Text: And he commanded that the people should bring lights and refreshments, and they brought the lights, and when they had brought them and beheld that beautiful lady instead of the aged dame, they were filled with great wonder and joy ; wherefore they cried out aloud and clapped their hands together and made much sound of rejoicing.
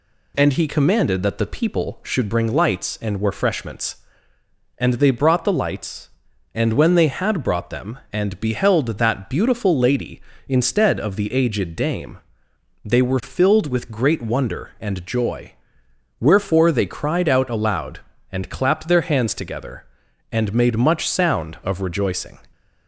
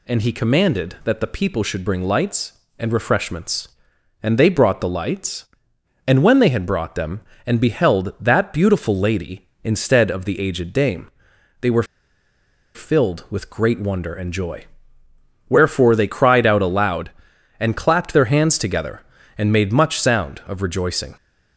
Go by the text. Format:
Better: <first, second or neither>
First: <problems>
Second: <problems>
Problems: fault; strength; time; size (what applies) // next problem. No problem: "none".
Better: first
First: none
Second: pauses between "were" and "filled"; noticeable; at 11.8 s; 0.91 s long